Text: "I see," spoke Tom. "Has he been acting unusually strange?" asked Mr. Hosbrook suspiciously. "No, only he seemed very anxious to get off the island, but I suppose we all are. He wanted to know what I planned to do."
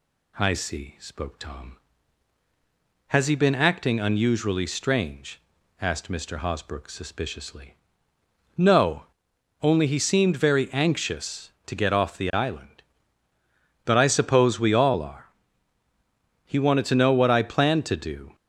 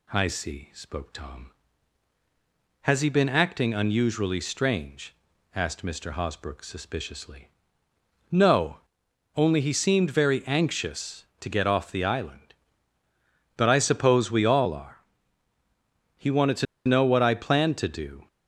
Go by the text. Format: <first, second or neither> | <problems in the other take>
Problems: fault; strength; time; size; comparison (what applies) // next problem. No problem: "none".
first | pauses between "to" and "know"; slight; at 16.6 s; 0.21 s long